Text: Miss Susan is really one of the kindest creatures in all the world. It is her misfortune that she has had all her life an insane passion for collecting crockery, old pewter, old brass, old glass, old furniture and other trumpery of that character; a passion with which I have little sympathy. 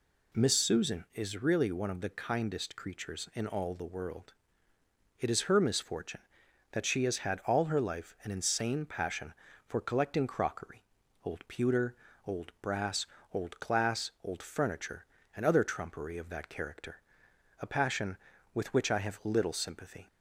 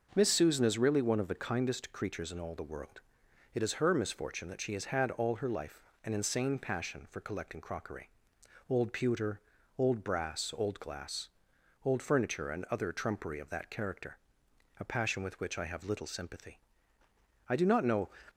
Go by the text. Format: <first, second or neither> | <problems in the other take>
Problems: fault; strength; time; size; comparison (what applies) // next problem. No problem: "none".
first | starts louder than the rest; noticeable; until 1.1 s; 6 dB // pauses between "life" and "an"; slight; at 5.8 s; 0.20 s long // goes on to say "I do not know"; noticeable; from 17.4 s on; 0.62 s long